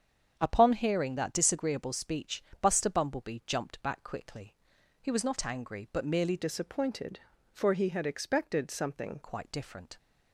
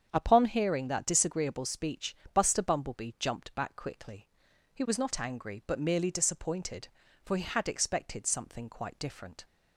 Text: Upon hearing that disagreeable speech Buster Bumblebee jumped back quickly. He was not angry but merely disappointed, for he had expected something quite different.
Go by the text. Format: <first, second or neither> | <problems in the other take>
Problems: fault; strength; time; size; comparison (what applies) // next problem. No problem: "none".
second | starts louder than the rest; strong; until 1.3 s; 8 dB; strong in the second // pauses between "speech" and "Buster"; slight; at 2.4 s; 0.18 s long; slight in the second // changes voice from "disappointed" to "something"; from 6.3 to 9.1 s; 2.8 s long